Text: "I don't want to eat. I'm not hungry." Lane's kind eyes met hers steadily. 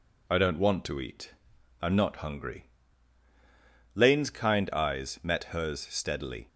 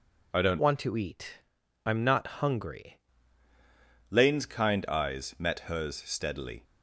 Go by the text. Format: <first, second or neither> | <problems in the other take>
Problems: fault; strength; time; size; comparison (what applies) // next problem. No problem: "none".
first | changes voice from "want" to "hungry"; from 0.5 to 2.9 s; 2.4 s long